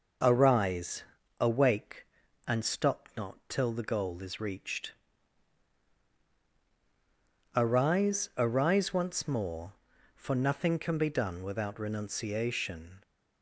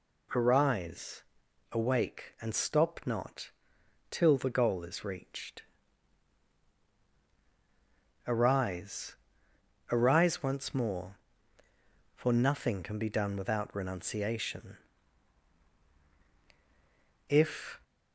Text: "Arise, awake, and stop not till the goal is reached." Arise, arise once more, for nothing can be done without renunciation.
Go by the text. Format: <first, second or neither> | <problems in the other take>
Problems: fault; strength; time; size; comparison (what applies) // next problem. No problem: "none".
first | pauses between "not" and "till"; noticeable; at 3.4 s; 0.62 s long // goes on to say "If"; from 17.2 s on; 0.52 s long